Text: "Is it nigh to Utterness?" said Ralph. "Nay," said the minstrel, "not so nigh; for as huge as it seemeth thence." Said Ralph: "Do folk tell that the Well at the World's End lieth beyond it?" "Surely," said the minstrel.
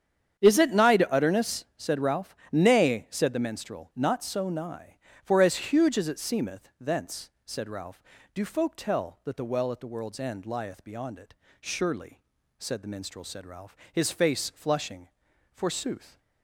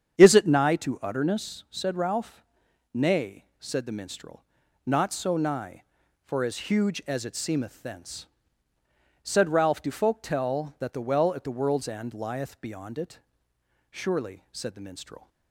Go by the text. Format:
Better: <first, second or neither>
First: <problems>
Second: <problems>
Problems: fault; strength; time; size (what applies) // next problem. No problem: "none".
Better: second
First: starts louder than the rest; strong; until 1.4 s; 8.5 dB // goes on to say "Said Ralph his face flushing Forsooth"; strong; from 13.2 s on; 2.9 s long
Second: starts louder than the rest; strong; until 1.2 s; 8 dB